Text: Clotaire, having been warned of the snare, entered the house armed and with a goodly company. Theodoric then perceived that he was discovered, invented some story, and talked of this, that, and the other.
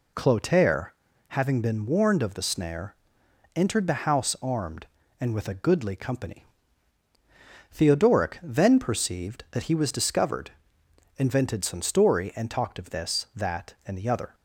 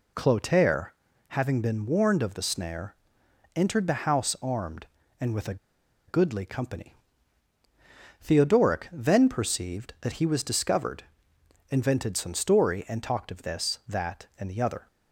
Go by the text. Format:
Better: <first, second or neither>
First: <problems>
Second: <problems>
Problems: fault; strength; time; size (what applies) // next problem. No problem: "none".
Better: first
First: none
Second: pauses between "a" and "goodly"; noticeable; at 5.5 s; 0.52 s long